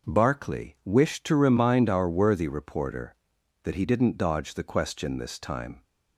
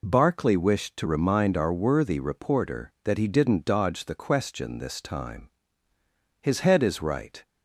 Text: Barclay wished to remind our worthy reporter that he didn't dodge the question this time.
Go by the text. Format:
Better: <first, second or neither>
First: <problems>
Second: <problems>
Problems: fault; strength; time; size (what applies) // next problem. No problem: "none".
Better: first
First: none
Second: goes on to say "His head is right"; noticeable; from 6.4 s on; 1.0 s long